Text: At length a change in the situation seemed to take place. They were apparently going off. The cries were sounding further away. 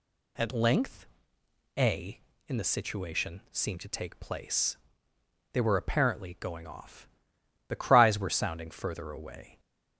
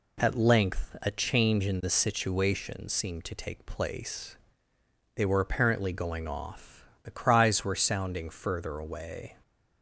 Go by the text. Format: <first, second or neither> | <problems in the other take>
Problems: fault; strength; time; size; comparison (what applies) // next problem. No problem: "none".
second | pauses between "length" and "a"; noticeable; at 1.0 s; 0.72 s long // skips "change"; at 2.3 s